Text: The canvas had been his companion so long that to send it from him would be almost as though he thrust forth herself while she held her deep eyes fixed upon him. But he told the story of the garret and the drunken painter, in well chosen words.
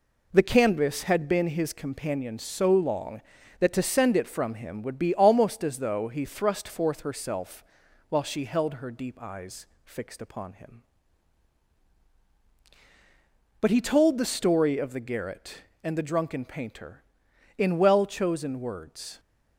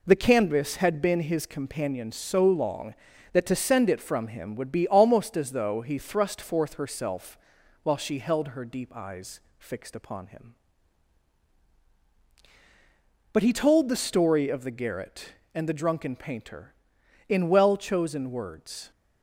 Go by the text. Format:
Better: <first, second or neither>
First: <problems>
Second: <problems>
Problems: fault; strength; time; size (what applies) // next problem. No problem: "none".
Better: neither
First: pauses between "herself" and "while"; noticeable; at 7.6 s; 0.46 s long // pauses between "eyes" and "fixed"; slight; at 9.6 s; 0.18 s long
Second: pauses between "herself" and "while"; noticeable; at 7.3 s; 0.46 s long // pauses between "eyes" and "fixed"; slight; at 9.3 s; 0.18 s long